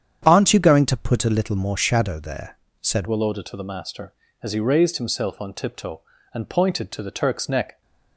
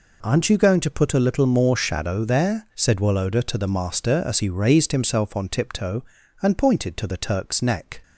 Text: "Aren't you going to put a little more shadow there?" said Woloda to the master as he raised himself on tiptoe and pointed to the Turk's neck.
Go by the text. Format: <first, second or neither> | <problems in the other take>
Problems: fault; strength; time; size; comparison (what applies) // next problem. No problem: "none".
second | starts louder than the rest; strong; until 1.2 s; 9 dB // changes voice at "Woloda"; from 3.0 s on; 4.8 s long